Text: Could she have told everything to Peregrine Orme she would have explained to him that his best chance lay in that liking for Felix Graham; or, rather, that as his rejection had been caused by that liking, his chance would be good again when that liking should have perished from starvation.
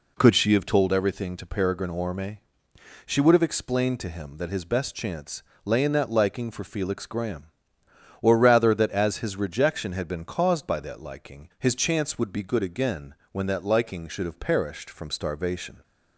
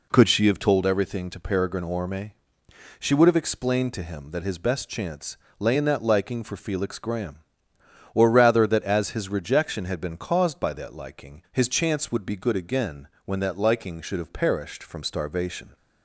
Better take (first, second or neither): neither